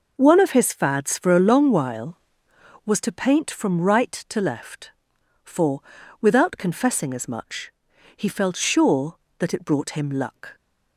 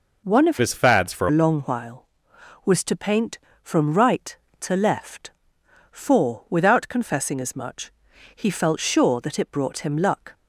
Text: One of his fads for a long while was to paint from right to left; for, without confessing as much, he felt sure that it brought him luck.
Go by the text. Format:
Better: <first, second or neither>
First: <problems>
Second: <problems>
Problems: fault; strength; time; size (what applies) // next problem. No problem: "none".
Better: first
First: none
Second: changes voice from "his" to "for"; from 0.5 to 1.2 s; 0.7 s long